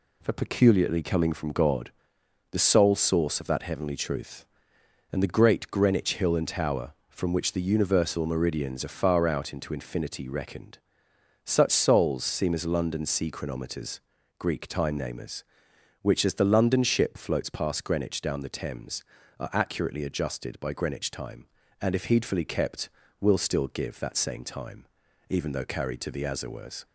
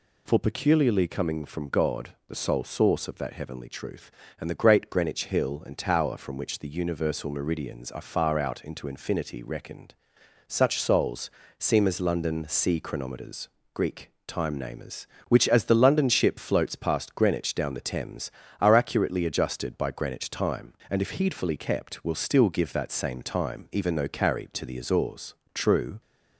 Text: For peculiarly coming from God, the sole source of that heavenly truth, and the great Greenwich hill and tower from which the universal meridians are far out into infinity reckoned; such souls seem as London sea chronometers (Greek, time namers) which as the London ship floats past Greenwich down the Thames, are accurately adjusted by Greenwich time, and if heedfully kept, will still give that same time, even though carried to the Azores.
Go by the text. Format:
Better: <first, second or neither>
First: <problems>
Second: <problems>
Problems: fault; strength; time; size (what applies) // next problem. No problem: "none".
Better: first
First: none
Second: pauses between "souls" and "seem"; slight; at 11.3 s; 0.30 s long // goes on to say "True"; slight; from 25.5 s on; 0.46 s long